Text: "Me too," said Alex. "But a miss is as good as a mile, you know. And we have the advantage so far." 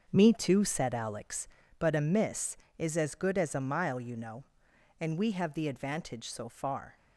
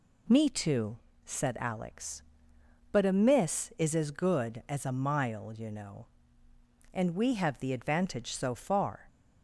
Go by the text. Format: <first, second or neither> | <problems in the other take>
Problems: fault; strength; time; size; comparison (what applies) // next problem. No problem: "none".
second | starts louder than the rest; until 1.7 s; 6.5 dB